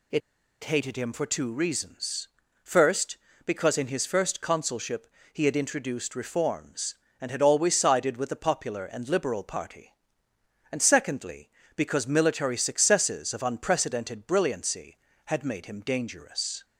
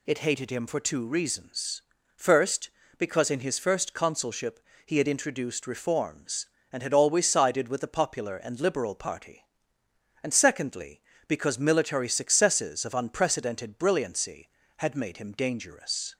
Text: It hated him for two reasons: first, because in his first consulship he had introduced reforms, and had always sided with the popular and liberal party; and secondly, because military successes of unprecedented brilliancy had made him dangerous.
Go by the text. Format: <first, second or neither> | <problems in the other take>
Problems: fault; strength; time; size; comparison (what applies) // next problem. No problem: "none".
second | pauses between "It" and "hated"; at 0.2 s; 0.44 s long // pauses between "consulship" and "he"; slight; at 5.0 s; 0.26 s long; slight in the second